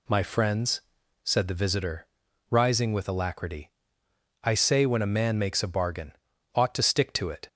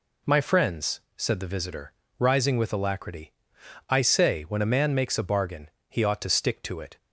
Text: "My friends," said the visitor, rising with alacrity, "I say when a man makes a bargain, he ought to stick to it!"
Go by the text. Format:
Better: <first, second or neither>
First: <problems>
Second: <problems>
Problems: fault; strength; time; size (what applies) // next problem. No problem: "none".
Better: second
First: skips "he"; at 6.3 s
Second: none